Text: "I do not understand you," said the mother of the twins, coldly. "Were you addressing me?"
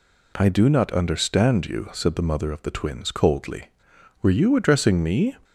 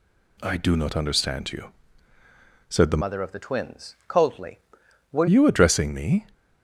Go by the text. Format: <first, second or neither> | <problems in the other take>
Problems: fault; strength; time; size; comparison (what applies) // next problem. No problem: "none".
first | changes voice from "mother" to "Were"; from 3.0 to 5.2 s; 2.2 s long